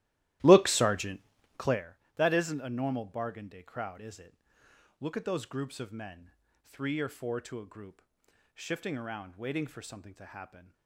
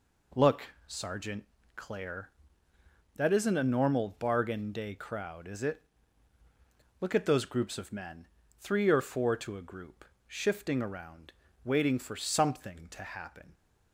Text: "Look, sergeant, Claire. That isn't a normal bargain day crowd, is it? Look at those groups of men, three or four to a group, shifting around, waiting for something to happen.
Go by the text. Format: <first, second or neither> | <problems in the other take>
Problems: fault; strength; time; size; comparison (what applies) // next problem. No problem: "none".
second | starts louder than the rest; strong; until 1.9 s; 15 dB